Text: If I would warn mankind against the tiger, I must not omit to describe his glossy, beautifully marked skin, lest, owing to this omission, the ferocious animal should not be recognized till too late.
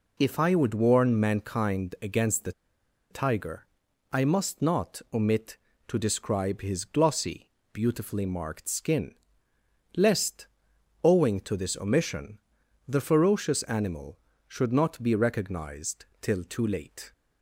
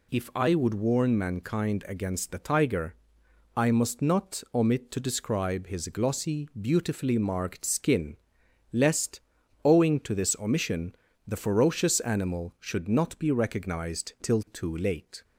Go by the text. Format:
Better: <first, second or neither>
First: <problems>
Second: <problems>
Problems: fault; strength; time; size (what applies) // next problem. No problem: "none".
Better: second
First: pauses between "the" and "tiger"; noticeable; at 2.5 s; 0.59 s long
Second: none